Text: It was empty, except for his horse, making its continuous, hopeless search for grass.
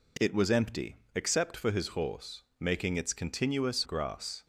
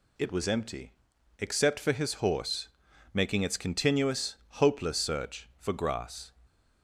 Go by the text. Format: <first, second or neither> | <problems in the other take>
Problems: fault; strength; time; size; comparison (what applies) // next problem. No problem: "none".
second | skips "hopeless search for"; at 3.8 s